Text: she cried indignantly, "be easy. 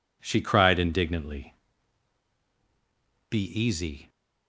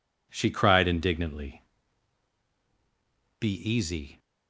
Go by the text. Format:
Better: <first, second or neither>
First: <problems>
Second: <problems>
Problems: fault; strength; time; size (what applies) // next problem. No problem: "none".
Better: neither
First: none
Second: none